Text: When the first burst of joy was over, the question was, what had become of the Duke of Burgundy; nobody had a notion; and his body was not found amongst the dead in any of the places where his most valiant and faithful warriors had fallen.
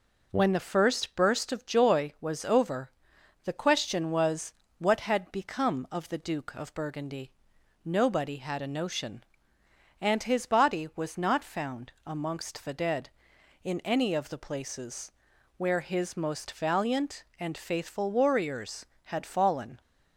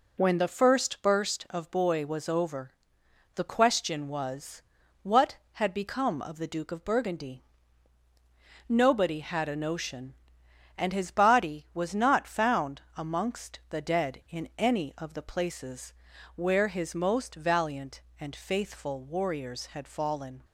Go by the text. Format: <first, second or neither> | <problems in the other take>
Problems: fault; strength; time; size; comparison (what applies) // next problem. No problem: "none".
first | says "boy" for "joy"; at 1.7 s // pauses between "found" and "amongst"; slight; at 12.8 s; 0.16 s long // pauses between "places" and "where"; at 15.9 s; 0.44 s long; also in the first